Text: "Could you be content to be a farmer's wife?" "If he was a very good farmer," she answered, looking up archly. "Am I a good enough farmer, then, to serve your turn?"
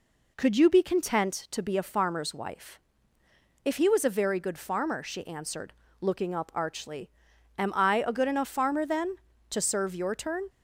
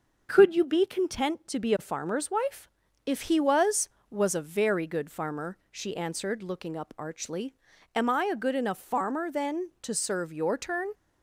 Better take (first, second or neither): first